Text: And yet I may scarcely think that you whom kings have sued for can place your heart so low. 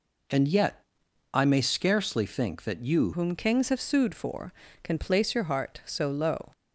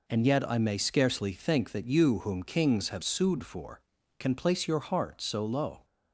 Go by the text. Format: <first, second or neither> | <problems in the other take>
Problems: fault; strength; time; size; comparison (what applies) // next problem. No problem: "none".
second | pauses between "yet" and "I"; noticeable; at 0.8 s; 0.52 s long // changes voice at "whom"; from 3.1 s on; 3.4 s long